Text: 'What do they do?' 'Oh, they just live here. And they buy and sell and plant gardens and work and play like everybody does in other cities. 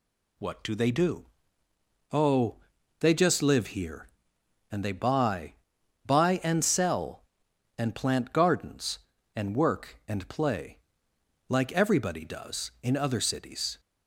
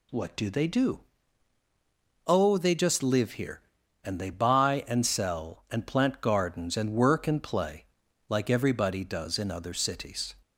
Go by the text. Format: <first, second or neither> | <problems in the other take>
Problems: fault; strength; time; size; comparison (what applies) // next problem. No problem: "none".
second | says "buy" twice; at 6.0 s // pauses between "play" and "like"; noticeable; at 10.7 s; 0.68 s long; noticeable in the second